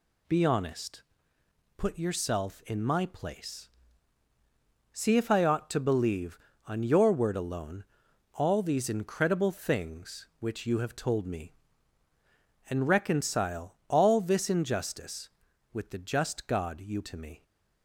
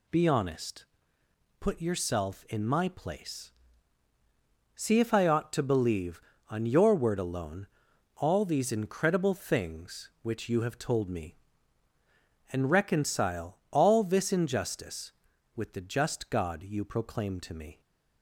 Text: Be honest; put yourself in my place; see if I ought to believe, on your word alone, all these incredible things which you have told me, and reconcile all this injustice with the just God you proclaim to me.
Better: second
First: skips "proclaim"; at 17.0 s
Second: none

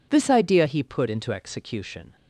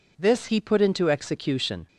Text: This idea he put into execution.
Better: first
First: none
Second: skips "idea"; at 0.4 s

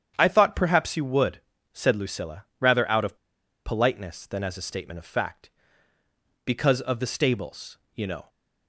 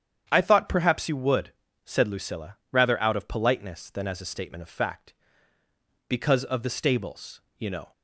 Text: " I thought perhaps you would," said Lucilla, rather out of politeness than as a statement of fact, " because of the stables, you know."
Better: second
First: starts louder than the rest; strong; until 1.1 s; 9 dB // pauses between "of" and "politeness"; noticeable; at 3.1 s; 0.49 s long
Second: starts louder than the rest; strong; until 1.2 s; 9 dB

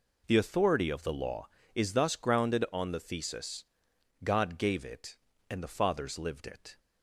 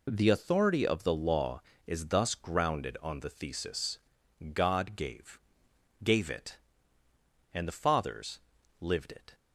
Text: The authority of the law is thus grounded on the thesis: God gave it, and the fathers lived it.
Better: first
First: none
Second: says "gave" twice; at 6.0 s // pauses between "fathers" and "lived"; at 8.3 s; 0.42 s long

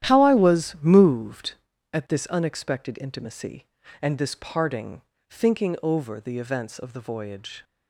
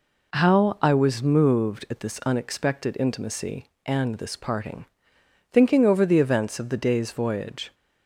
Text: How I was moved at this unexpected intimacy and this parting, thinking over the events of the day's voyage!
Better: second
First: starts louder than the rest; strong; until 1.1 s; 11 dB // skips "day's"; at 6.9 s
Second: none

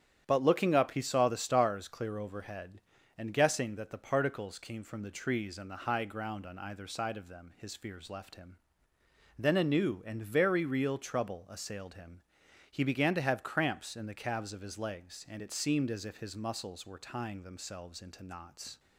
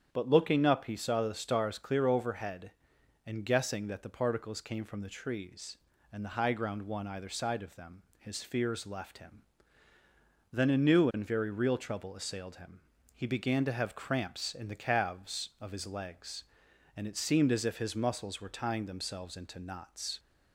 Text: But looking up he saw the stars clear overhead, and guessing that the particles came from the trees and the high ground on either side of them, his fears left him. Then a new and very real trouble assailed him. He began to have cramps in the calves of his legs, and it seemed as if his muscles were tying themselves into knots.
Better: first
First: starts louder than the rest; strong; until 1.2 s; 9.5 dB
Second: starts louder than the rest; strong; until 1.1 s; 8.5 dB // says "one" for "on"; at 6.8 s

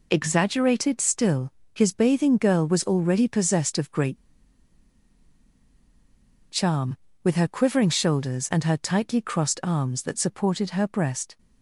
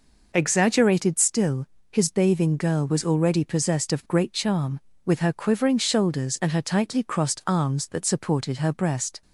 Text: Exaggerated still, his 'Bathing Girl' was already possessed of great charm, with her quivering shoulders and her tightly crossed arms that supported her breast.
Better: second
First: pauses between "great" and "charm"; strong; at 4.1 s; 2.3 s long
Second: none

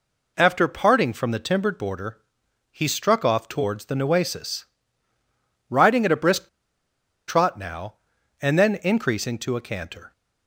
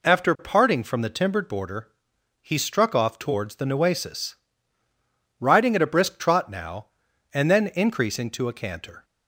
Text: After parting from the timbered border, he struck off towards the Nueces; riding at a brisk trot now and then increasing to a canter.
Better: second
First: pauses between "brisk" and "trot"; noticeable; at 6.4 s; 0.79 s long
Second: none

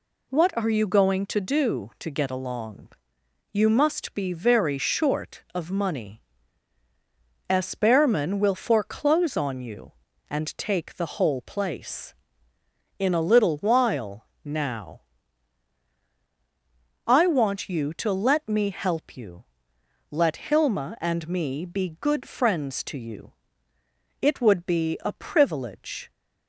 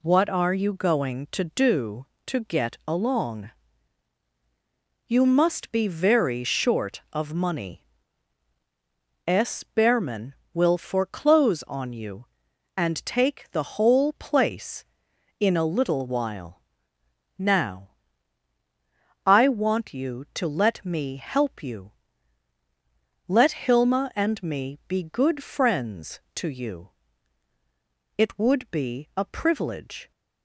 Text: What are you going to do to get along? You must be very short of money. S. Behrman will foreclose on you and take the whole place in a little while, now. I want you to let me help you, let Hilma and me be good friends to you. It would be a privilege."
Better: neither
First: none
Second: none

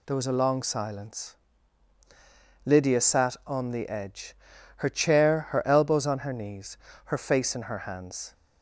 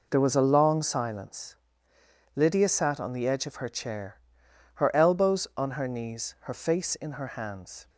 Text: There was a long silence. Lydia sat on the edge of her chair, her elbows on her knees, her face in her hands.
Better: second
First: skips "of"; at 4.5 s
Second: none

